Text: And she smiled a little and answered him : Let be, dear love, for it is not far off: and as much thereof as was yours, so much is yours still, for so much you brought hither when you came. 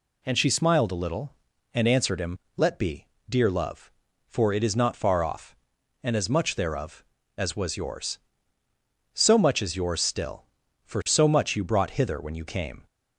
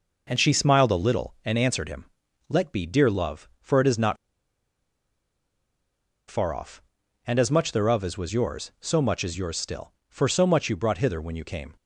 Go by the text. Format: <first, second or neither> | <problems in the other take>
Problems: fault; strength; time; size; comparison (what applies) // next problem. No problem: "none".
first | pauses between "not" and "far"; strong; at 4.1 s; 2.1 s long